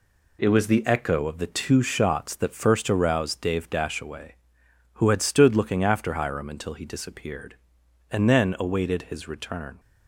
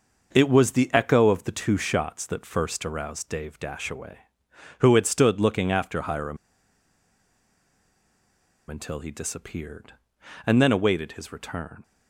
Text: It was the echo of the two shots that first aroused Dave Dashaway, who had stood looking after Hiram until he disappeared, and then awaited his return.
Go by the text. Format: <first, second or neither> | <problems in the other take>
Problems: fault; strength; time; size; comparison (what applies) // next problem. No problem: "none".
first | starts louder than the rest; noticeable; until 1.3 s; 6 dB // pauses between "Hiram" and "until"; strong; at 6.3 s; 2.3 s long